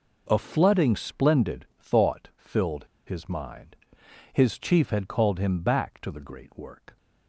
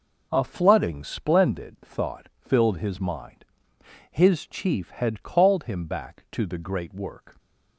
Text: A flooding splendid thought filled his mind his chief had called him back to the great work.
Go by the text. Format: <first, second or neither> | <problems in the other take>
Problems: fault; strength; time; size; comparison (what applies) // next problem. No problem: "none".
second | pauses between "filled" and "his"; slight; at 2.8 s; 0.25 s long // pauses between "mind" and "his"; noticeable; at 3.7 s; 0.58 s long; noticeable in the second